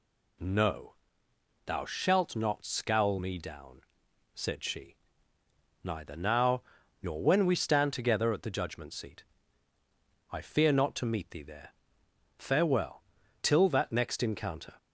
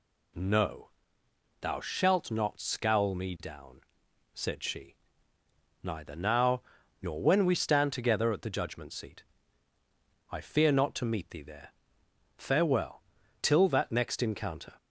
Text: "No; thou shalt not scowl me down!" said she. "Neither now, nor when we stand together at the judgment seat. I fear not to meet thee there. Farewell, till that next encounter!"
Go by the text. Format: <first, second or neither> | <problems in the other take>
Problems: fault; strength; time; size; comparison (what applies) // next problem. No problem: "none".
neither | none